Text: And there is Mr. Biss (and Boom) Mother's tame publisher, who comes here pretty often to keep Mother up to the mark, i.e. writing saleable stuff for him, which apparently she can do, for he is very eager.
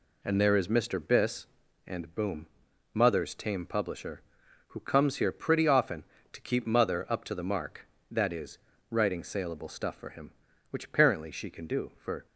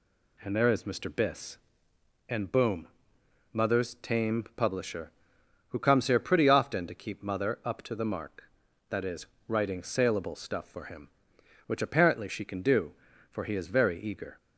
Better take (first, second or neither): second